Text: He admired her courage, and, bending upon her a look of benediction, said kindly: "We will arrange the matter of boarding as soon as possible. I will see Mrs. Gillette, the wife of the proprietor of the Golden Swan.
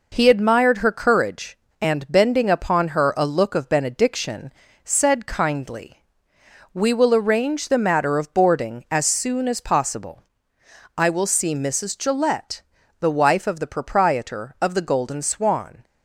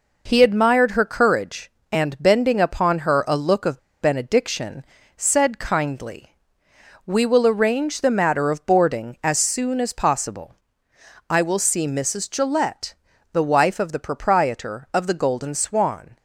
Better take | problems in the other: first | pauses between "of" and "benediction"; slight; at 3.7 s; 0.23 s long

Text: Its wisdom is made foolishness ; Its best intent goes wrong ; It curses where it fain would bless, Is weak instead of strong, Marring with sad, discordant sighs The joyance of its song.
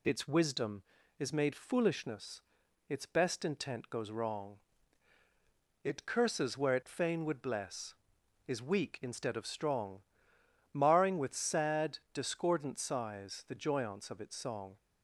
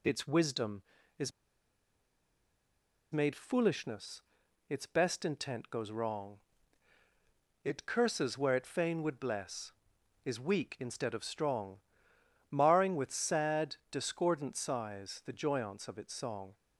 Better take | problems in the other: first | pauses between "is" and "made"; strong; at 1.3 s; 1.8 s long

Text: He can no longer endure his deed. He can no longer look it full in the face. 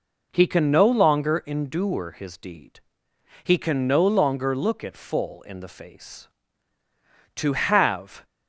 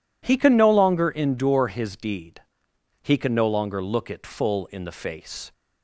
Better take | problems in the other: second | goes on to say "To have"; noticeable; from 7.3 s on; 0.88 s long

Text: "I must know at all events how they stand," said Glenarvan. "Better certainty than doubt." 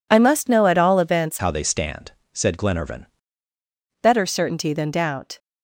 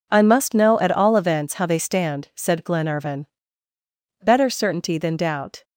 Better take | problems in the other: second | changes voice from "how" to "Glenarvan"; from 1.3 to 3.0 s; 1.7 s long

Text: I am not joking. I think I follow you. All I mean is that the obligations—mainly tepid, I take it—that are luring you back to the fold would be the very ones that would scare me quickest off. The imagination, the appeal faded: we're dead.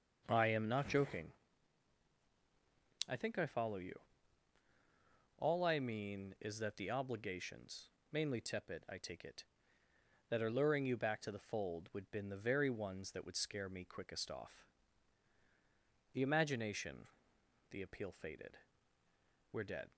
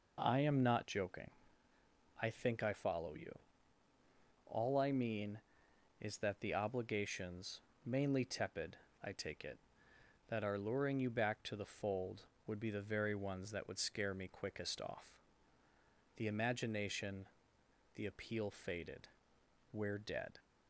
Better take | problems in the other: second | says "been" for "be"; at 12.0 s

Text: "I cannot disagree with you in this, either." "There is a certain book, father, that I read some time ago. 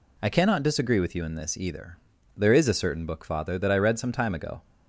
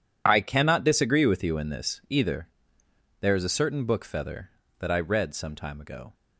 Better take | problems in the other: first | says "feather" for "father"; at 4.0 s

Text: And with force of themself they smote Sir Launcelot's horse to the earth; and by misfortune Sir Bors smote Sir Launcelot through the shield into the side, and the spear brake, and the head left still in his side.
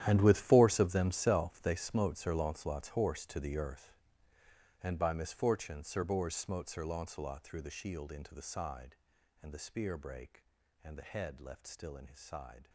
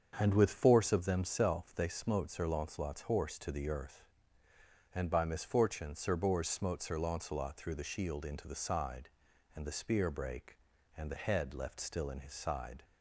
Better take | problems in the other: second | gets quieter; strong; throughout; 16 dB // starts louder than the rest; strong; until 1.0 s; 11.5 dB; strong in the second

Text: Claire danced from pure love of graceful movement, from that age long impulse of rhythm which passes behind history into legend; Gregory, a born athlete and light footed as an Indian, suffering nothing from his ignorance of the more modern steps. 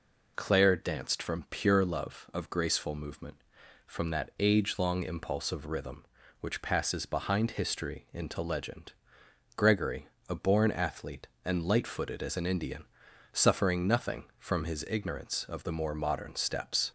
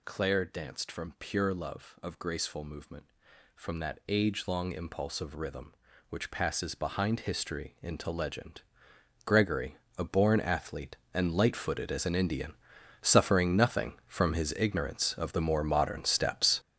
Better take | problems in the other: first | gets louder; strong; throughout; 9.5 dB

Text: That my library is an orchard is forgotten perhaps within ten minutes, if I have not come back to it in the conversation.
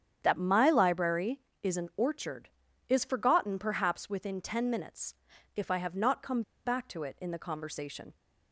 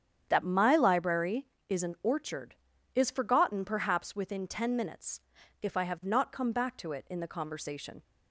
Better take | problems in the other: second | starts louder than the rest; strong; until 1.2 s; 9 dB; strong in the second // pauses between "come" and "back"; slight; at 6.4 s; 0.23 s long

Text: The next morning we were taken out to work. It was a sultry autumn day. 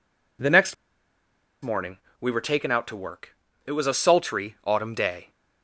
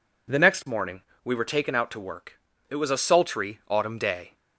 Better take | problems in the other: second | pauses between "next" and "morning"; noticeable; at 0.7 s; 0.88 s long // pauses between "morning" and "we"; slight; at 1.9 s; 0.24 s long; slight in the second

